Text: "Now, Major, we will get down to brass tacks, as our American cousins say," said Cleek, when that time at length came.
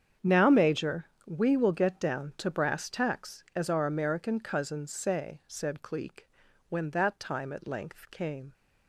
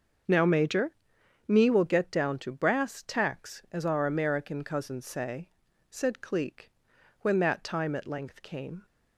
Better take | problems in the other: first | starts louder than the rest; until 1.8 s; 6.5 dB; strong in the first // says "me" for "we"; at 1.4 s

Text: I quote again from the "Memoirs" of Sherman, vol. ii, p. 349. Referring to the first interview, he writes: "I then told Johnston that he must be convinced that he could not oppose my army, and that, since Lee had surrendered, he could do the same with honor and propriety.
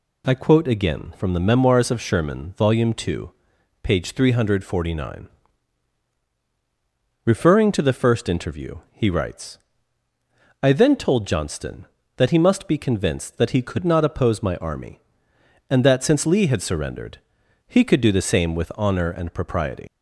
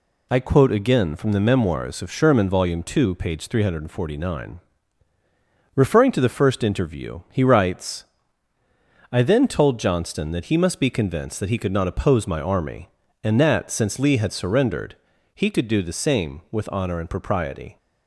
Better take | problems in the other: second | leaves "propriety" unfinished; at 19.8 s; 85 ms

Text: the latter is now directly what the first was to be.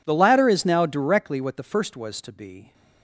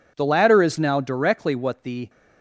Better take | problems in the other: first | stops before "first was to be"; at 2.0 s

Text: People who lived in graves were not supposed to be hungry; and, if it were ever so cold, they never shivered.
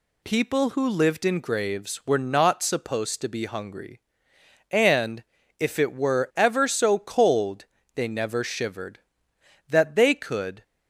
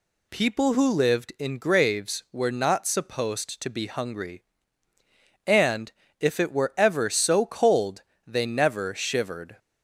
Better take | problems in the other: second | goes on to say "That they could"; noticeable; from 9.6 s on; 0.94 s long

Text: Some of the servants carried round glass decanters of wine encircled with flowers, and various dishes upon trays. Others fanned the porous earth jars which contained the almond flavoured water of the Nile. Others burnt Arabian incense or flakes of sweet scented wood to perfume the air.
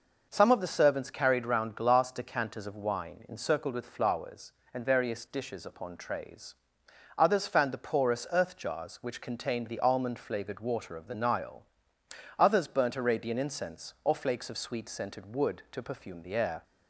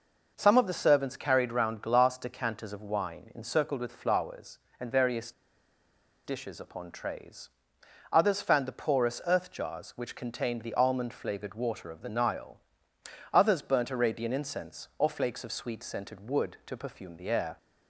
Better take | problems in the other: first | pauses between "various" and "dishes"; noticeable; at 5.3 s; 0.93 s long

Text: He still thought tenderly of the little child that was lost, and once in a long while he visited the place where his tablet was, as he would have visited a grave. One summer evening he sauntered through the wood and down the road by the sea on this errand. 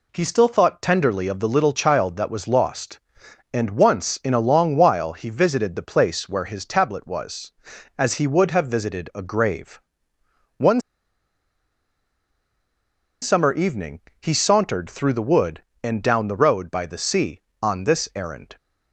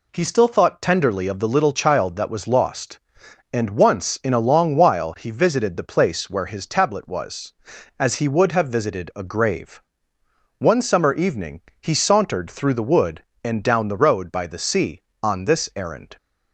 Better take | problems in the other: second | pauses between "One" and "summer"; strong; at 10.8 s; 2.4 s long // pauses between "evening" and "he"; slight; at 13.9 s; 0.20 s long; slight in the second

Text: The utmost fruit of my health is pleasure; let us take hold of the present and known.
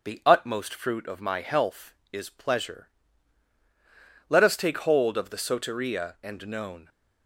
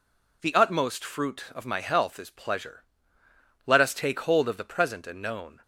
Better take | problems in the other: second | starts louder than the rest; noticeable; until 1.0 s; 6 dB // says "soteria" for "present"; at 5.3 s

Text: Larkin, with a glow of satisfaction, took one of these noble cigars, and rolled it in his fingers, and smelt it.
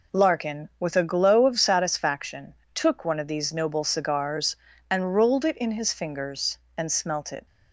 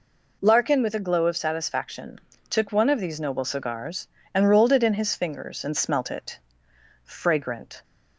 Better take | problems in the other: first | goes on to say "Fragrant"; noticeable; from 7.0 s on; 0.80 s long

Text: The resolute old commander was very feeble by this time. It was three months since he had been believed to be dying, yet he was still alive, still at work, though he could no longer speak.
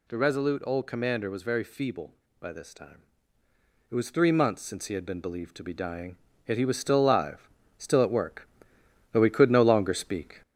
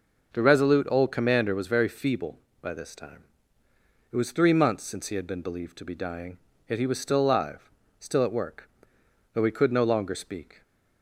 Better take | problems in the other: second | gets louder; slight; throughout; 3 dB

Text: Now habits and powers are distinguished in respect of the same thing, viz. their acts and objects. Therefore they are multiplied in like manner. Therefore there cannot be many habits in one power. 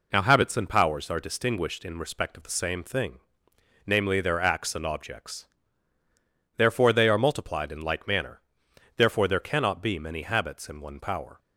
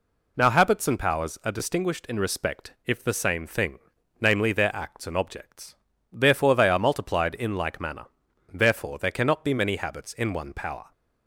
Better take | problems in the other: first | says "if" for "of"; at 2.8 s

